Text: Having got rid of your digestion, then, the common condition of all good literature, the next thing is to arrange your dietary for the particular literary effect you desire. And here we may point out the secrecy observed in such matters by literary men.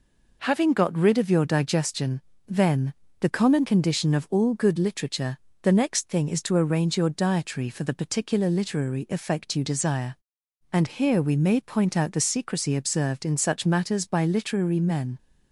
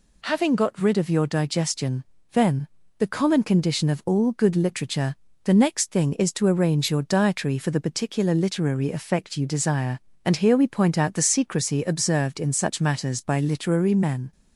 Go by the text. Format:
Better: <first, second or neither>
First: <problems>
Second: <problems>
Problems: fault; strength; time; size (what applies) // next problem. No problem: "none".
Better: first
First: none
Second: skips "may"; at 10.6 s